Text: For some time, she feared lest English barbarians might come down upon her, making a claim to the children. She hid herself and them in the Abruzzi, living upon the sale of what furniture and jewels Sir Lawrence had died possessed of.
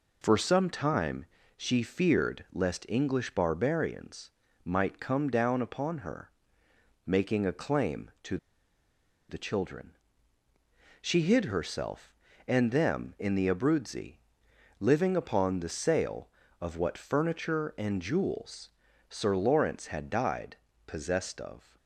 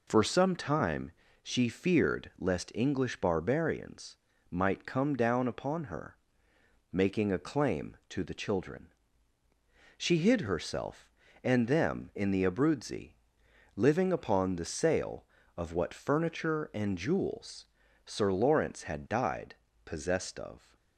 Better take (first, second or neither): second